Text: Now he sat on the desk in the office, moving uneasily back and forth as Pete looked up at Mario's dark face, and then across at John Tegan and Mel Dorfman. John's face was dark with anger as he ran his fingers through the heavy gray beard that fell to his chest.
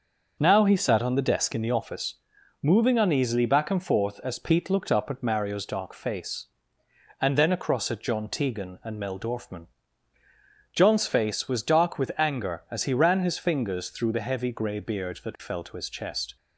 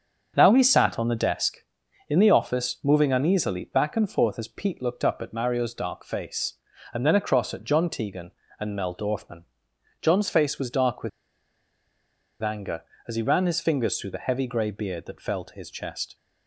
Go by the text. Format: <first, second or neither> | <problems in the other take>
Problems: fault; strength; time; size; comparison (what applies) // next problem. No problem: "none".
first | starts louder than the rest; until 1.3 s; 6.5 dB; also in the first // pauses between "with" and "anger"; strong; at 11.0 s; 1.3 s long